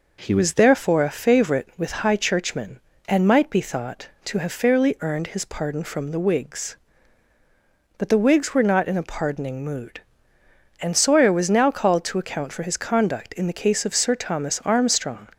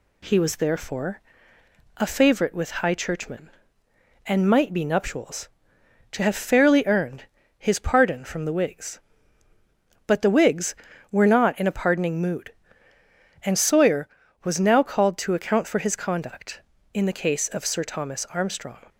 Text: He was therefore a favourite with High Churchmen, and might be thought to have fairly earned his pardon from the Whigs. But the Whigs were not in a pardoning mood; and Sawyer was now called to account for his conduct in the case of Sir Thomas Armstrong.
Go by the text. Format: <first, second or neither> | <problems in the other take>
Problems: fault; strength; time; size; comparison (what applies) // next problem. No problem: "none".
first | pauses between "therefore" and "a"; noticeable; at 1.1 s; 0.78 s long // says "nuptials" for "thought"; at 4.8 s // pauses between "earned" and "his"; slight; at 7.2 s; 0.32 s long